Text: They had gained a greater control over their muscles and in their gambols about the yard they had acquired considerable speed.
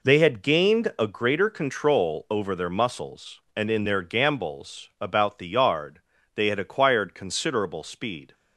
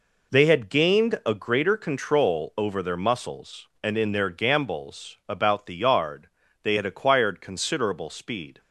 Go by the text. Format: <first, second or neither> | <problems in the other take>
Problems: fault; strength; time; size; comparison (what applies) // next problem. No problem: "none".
neither | pauses between "yard" and "they"; slight; the same in both